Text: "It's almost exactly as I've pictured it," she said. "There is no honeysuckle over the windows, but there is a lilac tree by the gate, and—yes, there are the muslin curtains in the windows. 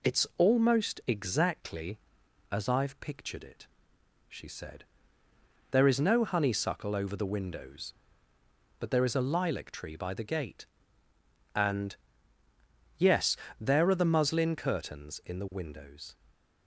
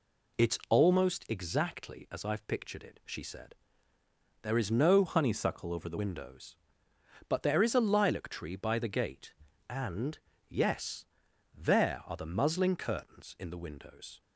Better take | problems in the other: first | changes voice from "honeysuckle" to "the"; from 5.0 to 5.9 s; 0.9 s long

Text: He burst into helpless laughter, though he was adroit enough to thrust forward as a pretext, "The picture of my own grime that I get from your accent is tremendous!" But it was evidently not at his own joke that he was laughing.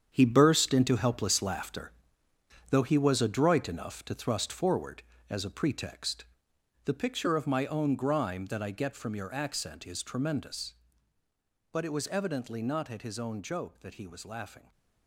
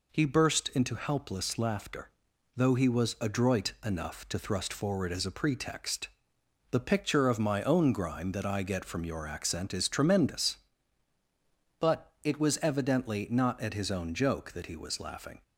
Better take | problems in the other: second | gets quieter; strong; throughout; 11 dB

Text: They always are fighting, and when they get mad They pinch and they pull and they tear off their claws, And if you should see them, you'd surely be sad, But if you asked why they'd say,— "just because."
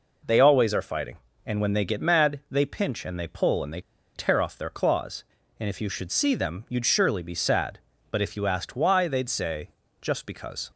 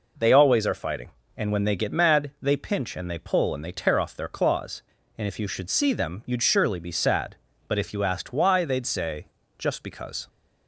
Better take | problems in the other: second | pauses between "they" and "tear"; slight; at 3.8 s; 0.33 s long

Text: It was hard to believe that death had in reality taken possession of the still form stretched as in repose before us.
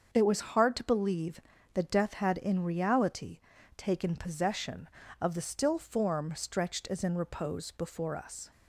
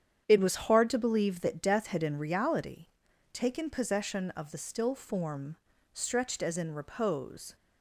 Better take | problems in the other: first | starts louder than the rest; strong; until 1.2 s; 8.5 dB; also in the first // pauses between "reality" and "taken"; noticeable; at 2.8 s; 0.48 s long; also in the first // pauses between "form" and "stretched"; slight; at 5.5 s; 0.36 s long // stops before "before us"; at 7.5 s

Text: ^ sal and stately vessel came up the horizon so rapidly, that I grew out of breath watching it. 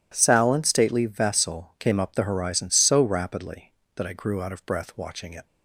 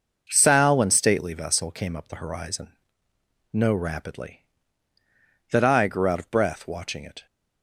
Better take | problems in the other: first | says "no" for "so"; at 3.4 s

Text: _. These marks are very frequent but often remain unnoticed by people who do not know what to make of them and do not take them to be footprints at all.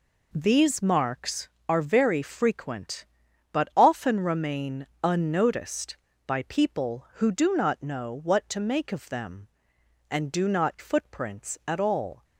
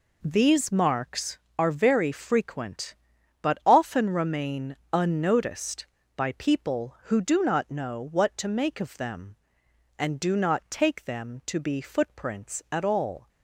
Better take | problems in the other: second | pauses between "remain" and "unnoticed"; slight; at 4.8 s; 0.18 s long; slight in the second // skips "take them to be"; at 10.7 s

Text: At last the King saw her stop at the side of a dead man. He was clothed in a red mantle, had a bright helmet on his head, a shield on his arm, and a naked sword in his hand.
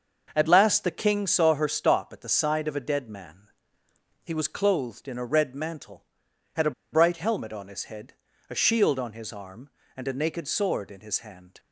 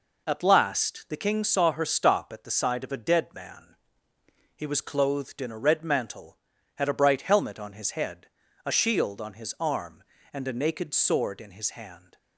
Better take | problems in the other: second | starts louder than the rest; noticeable; until 1.3 s; 6 dB // pauses between "a" and "bright"; slight; at 6.7 s; 0.21 s long

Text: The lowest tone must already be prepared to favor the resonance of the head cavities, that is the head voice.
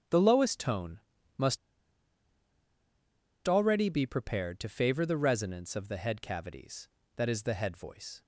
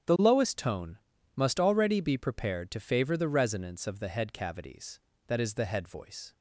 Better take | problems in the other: second | starts louder than the rest; strong; until 1.4 s; 9.5 dB; strong in the second // pauses between "tone" and "must"; slight; at 1.0 s; 0.36 s long; slight in the second // pauses between "must" and "already"; strong; at 1.5 s; 1.9 s long

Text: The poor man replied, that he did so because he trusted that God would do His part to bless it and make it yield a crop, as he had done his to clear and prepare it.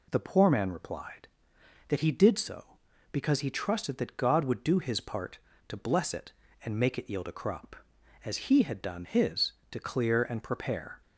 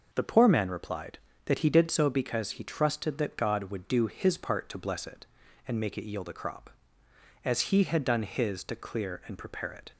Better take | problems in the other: second | stops before "it"; at 11.0 s

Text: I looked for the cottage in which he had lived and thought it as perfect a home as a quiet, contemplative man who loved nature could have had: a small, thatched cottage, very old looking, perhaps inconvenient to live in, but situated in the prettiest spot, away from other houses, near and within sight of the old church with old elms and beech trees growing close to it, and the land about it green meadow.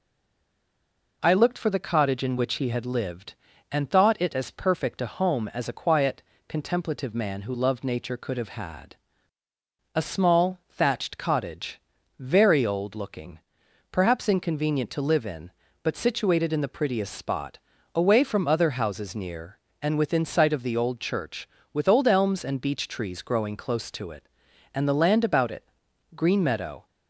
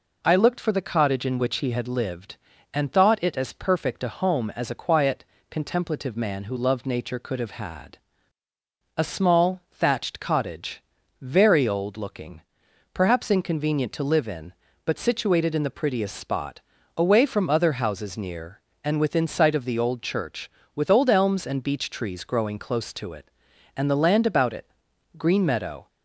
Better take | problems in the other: second | stays silent before the first word; noticeable; until 1.2 s; 1.2 s long // pauses between "it" and "green"; noticeable; at 25.6 s; 0.48 s long; noticeable in the second

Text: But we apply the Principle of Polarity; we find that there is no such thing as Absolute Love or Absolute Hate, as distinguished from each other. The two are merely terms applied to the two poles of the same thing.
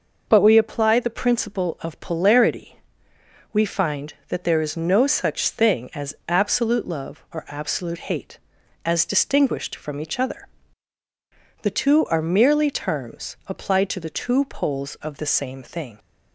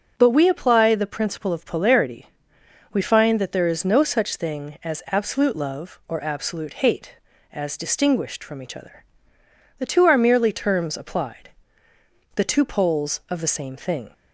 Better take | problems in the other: first | starts louder than the rest; noticeable; until 1.1 s; 6 dB // skips "to"; at 11.9 s

